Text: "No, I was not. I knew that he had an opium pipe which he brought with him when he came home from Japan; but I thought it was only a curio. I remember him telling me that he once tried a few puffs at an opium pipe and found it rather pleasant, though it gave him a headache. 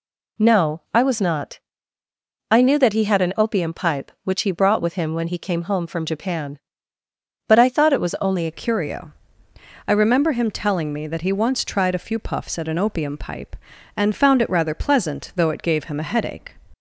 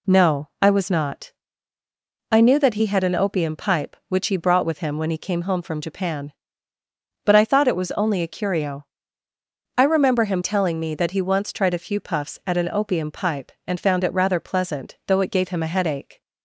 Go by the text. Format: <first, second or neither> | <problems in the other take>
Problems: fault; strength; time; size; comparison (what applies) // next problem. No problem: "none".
second | changes voice at "curio"; from 8.5 s on; 8.0 s long